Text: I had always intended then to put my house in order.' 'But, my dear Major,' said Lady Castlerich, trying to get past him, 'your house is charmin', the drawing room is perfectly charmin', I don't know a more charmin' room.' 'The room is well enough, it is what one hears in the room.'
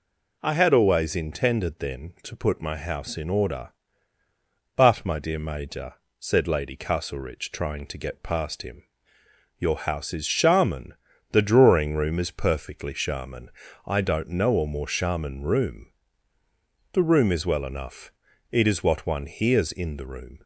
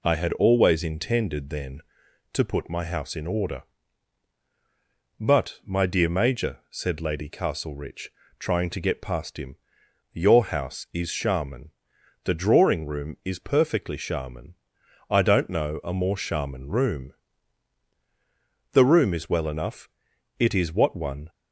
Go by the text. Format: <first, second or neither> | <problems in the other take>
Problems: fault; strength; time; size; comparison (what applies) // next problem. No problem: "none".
first | stops before "hears in the room"; at 21.2 s